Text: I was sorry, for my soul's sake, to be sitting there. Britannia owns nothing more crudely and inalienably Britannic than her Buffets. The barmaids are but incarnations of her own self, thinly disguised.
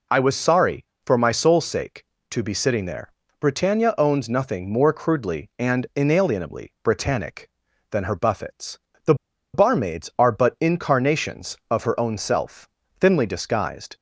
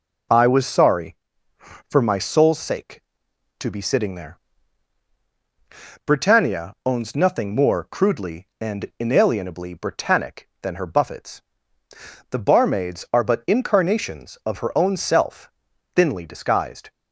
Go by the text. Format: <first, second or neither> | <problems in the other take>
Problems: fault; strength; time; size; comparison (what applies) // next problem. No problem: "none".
second | pauses between "The" and "barmaids"; at 9.1 s; 0.39 s long